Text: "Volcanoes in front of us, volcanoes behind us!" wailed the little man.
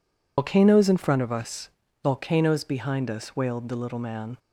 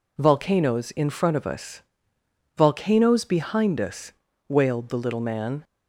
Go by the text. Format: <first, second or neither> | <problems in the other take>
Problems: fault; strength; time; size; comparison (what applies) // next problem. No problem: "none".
second | loses the start of "Volcanoes"; at 0.3 s; 115 ms